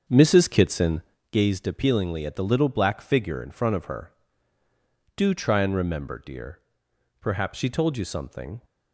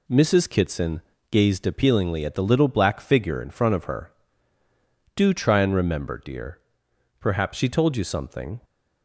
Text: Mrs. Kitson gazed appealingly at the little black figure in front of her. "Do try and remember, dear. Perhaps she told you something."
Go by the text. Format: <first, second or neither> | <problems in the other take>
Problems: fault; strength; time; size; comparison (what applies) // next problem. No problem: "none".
second | starts louder than the rest; until 1.2 s; 7 dB // pauses between "Kitson" and "gazed"; slight; at 1.0 s; 0.30 s long; slight in the second